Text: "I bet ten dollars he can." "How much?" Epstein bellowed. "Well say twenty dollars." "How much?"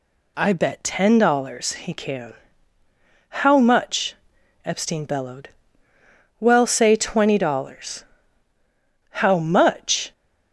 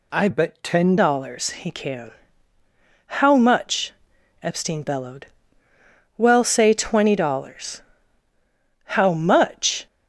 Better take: first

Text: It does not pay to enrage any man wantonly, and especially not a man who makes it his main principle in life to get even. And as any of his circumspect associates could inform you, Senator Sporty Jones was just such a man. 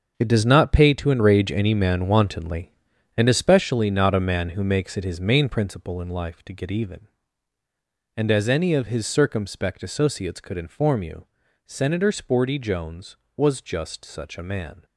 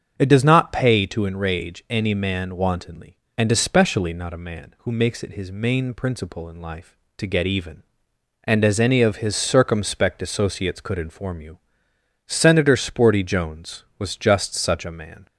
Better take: second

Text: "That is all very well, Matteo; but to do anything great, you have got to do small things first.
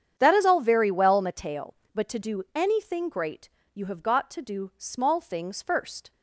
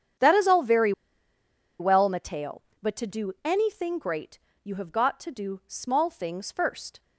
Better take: first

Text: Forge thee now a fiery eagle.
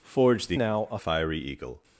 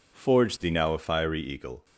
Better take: second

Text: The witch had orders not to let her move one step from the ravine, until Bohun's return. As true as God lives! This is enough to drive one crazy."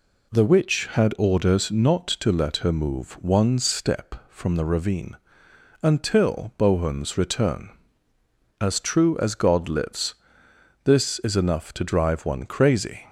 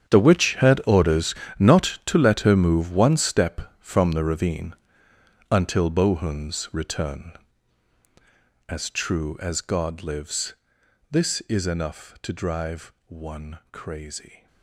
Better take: first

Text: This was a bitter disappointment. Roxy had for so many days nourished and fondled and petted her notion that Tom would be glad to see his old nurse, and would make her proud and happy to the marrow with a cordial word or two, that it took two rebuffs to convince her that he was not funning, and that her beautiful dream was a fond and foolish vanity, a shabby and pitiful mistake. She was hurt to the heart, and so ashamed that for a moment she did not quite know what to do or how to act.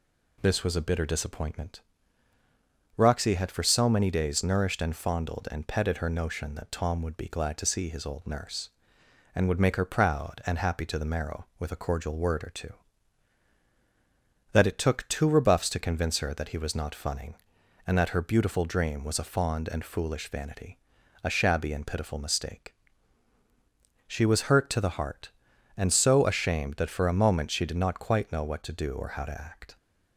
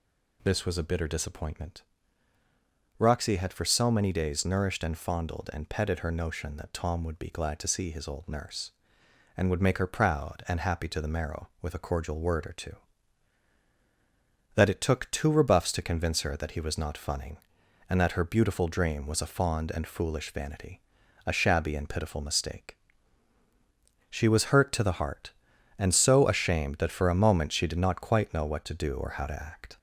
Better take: first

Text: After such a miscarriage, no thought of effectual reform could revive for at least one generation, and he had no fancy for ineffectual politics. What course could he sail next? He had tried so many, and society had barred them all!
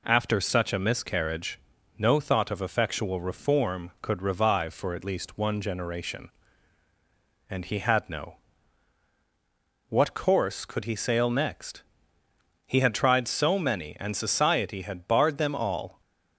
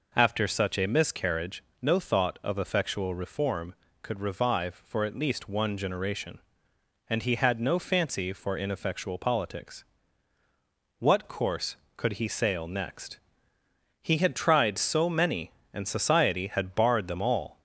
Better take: second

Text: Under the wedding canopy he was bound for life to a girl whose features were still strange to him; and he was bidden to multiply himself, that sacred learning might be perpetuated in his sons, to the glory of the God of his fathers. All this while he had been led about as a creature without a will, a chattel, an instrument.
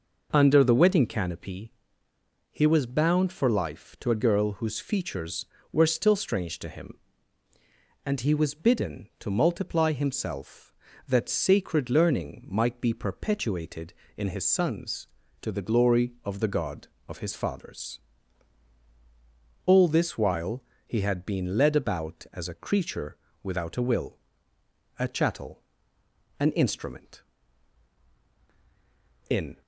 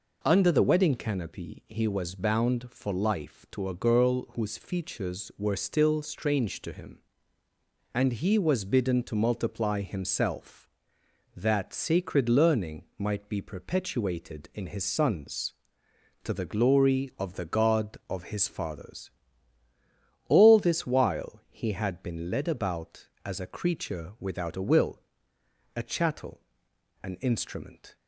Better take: second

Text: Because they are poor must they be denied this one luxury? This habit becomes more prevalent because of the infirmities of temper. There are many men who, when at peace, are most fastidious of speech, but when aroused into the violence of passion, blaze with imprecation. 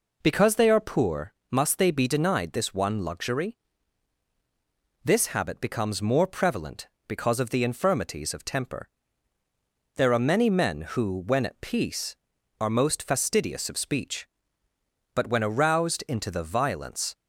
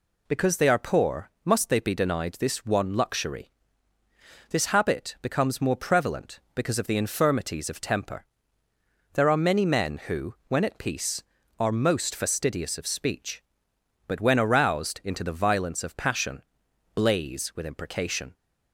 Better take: second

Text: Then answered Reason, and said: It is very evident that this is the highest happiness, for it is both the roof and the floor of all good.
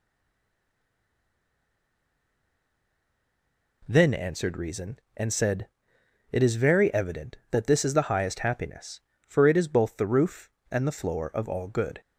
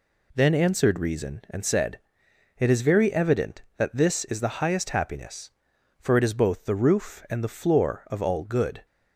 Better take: second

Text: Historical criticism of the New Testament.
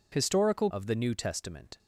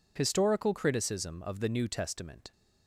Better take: second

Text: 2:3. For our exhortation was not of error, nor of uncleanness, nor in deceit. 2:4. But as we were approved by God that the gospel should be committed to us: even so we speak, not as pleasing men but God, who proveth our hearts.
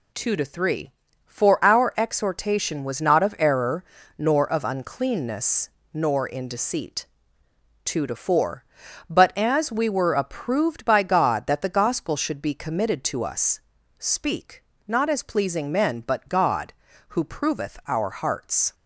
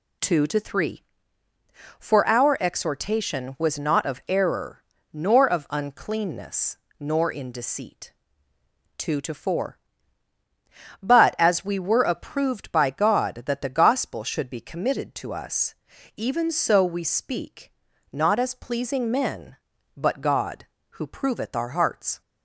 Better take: second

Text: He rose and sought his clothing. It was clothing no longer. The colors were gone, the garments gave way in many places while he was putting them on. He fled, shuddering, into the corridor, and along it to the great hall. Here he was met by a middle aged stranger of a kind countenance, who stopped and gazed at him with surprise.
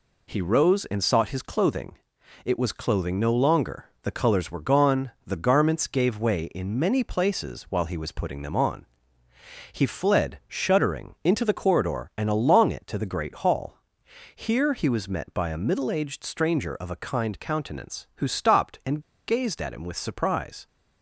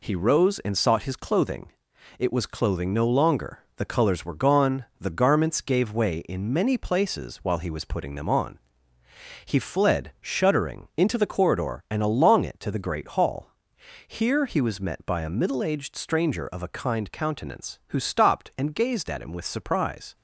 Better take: second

